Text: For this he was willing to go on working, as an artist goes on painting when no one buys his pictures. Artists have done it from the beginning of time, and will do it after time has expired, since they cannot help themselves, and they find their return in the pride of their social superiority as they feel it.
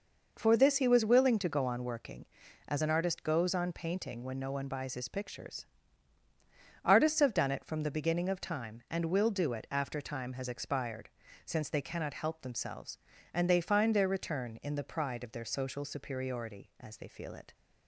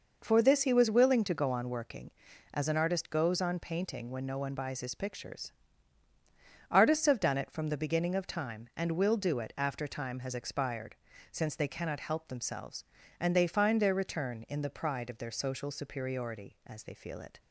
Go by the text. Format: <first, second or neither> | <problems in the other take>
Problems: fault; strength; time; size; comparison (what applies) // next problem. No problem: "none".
neither | none